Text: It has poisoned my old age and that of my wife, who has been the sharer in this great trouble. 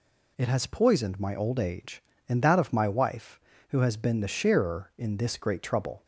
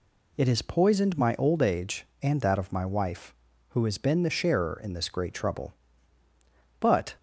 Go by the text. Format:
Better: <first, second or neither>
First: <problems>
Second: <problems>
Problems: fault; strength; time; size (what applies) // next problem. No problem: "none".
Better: first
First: none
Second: goes on to say "But"; slight; from 6.7 s on; 0.36 s long